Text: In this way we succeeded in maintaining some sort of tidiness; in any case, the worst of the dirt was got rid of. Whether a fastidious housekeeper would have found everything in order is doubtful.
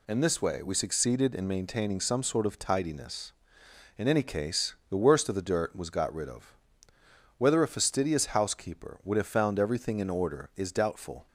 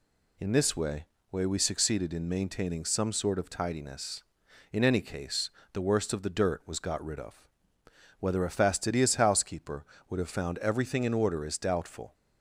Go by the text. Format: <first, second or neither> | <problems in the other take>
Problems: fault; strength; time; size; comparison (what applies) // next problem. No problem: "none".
first | says "way" twice; at 1.3 s